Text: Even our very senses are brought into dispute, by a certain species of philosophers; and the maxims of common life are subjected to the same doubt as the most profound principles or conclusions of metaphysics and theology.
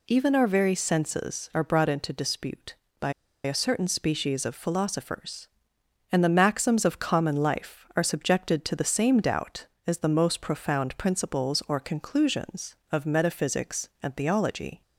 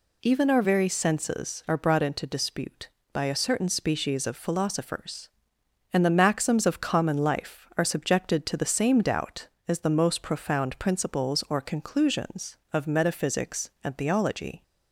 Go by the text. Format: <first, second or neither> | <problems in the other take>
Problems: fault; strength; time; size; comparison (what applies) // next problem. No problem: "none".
second | pauses between "by" and "a"; slight; at 3.1 s; 0.32 s long